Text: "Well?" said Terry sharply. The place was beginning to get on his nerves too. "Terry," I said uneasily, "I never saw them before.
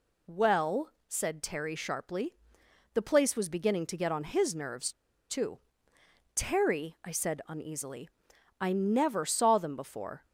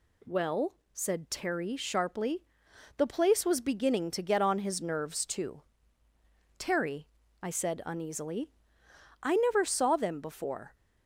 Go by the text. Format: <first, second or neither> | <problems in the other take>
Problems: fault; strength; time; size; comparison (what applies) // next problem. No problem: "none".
second | pauses between "nerves" and "too"; at 4.9 s; 0.37 s long